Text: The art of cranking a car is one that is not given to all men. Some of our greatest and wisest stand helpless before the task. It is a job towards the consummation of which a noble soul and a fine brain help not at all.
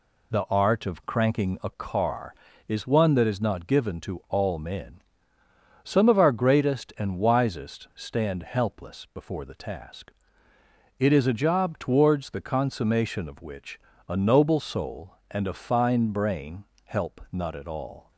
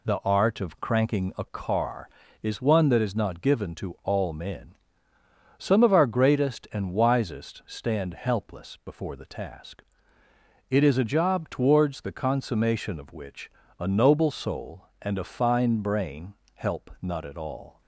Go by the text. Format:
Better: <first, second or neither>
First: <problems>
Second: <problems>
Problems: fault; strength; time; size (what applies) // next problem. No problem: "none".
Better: neither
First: pauses between "which" and "a"; slight; at 13.7 s; 0.30 s long // pauses between "brain" and "help"; slight; at 16.6 s; 0.18 s long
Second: pauses between "which" and "a"; slight; at 13.4 s; 0.30 s long // pauses between "brain" and "help"; slight; at 16.3 s; 0.18 s long